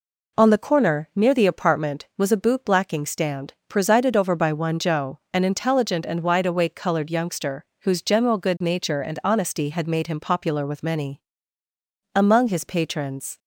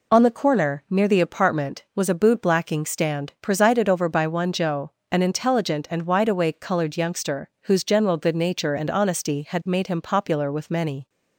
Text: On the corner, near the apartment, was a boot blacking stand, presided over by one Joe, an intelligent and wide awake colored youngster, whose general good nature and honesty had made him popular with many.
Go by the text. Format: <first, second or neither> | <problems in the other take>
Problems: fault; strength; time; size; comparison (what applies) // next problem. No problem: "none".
second | goes on to say "Among his patrons"; noticeable; from 12.1 s on; 1.2 s long